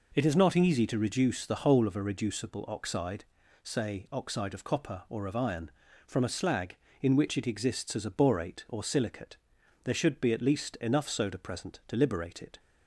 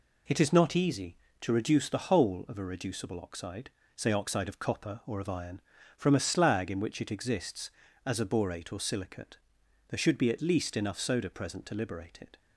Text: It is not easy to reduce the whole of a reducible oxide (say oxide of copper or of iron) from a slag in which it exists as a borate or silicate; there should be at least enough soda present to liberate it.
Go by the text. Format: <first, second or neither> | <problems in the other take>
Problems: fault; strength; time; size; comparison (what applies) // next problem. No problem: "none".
neither | none